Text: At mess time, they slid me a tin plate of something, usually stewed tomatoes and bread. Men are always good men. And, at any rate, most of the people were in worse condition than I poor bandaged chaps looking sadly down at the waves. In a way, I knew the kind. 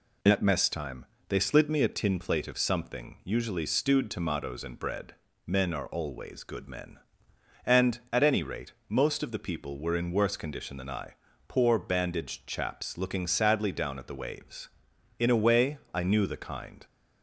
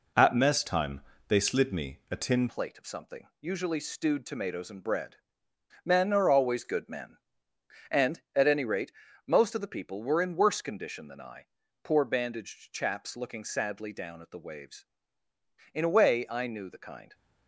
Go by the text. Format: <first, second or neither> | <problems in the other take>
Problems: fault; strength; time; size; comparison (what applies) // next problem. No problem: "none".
first | changes voice at "plate"; from 2.4 s on; 14.7 s long // pauses between "I" and "poor"; at 11.4 s; 0.38 s long; slight in the first